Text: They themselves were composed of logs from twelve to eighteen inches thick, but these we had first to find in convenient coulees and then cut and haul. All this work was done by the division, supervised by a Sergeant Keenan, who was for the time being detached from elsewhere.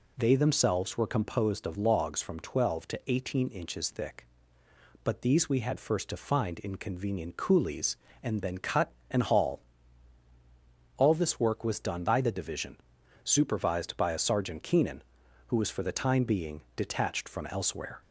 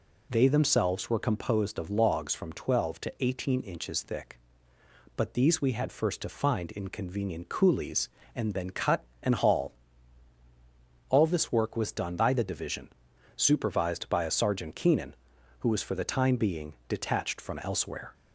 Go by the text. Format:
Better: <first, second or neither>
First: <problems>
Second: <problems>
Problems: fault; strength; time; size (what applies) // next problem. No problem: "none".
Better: neither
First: none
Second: none